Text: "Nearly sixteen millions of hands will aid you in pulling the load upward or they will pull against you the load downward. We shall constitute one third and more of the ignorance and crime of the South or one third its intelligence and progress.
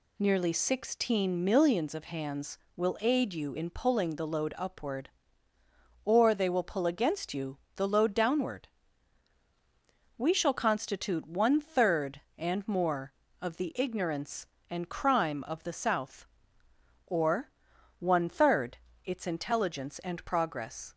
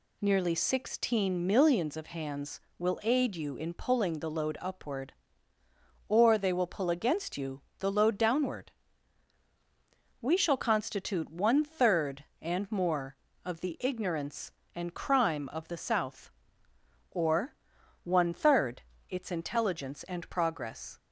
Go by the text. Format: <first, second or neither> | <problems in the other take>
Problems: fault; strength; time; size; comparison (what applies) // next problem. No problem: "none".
neither | pauses between "you" and "the"; slight; the same in both // pauses between "or" and "one"; noticeable; the same in both // pauses between "third" and "its"; slight; the same in both